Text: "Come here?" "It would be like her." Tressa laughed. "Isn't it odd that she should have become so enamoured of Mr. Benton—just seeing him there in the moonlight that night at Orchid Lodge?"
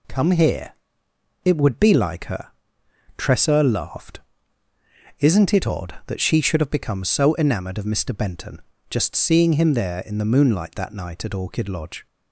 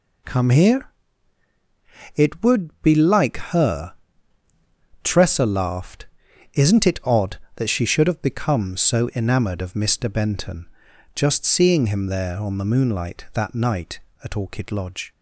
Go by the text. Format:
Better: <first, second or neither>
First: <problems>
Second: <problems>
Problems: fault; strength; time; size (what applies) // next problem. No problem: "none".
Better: first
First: none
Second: pauses between "like" and "her"; slight; at 3.3 s; 0.18 s long // says "on" for "in"; at 12.3 s